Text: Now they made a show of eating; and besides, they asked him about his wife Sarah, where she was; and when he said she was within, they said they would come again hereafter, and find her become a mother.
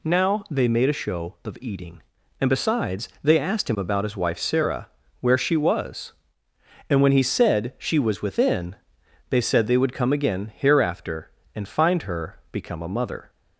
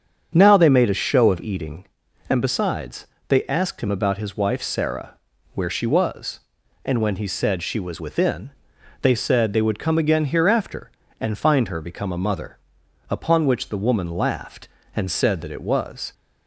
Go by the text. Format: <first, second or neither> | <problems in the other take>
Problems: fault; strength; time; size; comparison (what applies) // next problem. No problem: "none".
first | starts louder than the rest; strong; until 1.3 s; 7.5 dB // goes on to say "Upon which the woman laughed and said that it was"; strong; from 13.0 s on; 3.0 s long